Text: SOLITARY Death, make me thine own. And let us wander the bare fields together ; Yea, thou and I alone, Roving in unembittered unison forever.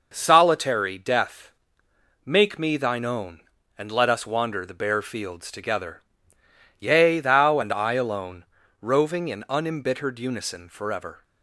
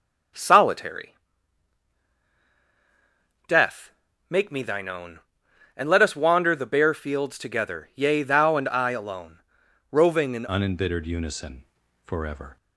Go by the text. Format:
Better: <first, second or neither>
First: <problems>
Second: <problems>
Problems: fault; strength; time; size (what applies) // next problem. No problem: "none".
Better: first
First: none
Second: starts louder than the rest; strong; until 3.6 s; 7.5 dB // pauses between "SOLITARY" and "Death"; strong; at 1.1 s; 2.3 s long // changes voice at "unembittered"; from 10.4 s on; 2.1 s long // pauses between "unison" and "forever"; at 11.6 s; 0.38 s long